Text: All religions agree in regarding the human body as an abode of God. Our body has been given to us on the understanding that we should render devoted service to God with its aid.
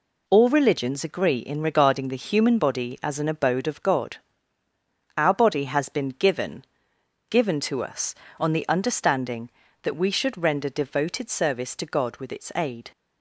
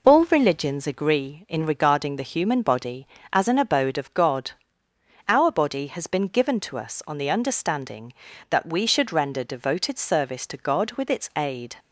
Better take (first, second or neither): second